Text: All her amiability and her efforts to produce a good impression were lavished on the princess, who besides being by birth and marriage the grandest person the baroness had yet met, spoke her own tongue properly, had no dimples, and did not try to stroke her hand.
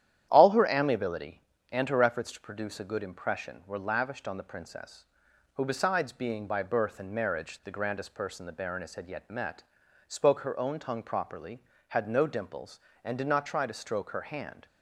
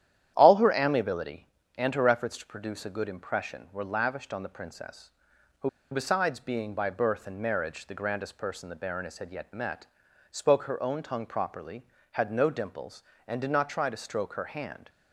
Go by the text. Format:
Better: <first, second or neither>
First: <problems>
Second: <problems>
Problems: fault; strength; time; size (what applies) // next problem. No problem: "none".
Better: first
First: starts louder than the rest; strong; until 1.3 s; 10.5 dB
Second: starts louder than the rest; strong; until 1.3 s; 10.5 dB // pauses between "who" and "besides"; slight; at 5.6 s; 0.22 s long